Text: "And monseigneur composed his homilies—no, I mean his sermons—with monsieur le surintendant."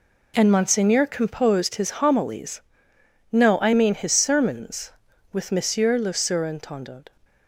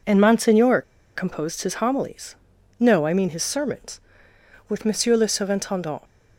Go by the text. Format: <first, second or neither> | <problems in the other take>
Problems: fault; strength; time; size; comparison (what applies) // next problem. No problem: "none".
first | pauses between "monseigneur" and "composed"; slight; at 0.8 s; 0.33 s long